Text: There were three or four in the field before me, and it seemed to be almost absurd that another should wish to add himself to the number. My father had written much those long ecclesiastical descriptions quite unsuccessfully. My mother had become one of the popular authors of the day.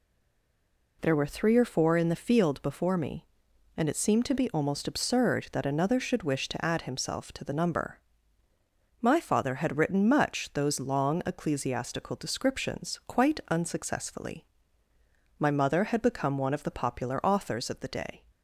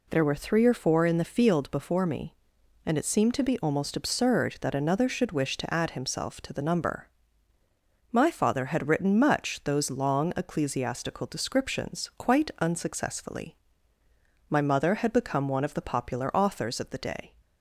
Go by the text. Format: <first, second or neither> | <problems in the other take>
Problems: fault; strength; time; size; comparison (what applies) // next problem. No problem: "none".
second | stays silent before the first word; until 1.0 s; 1.0 s long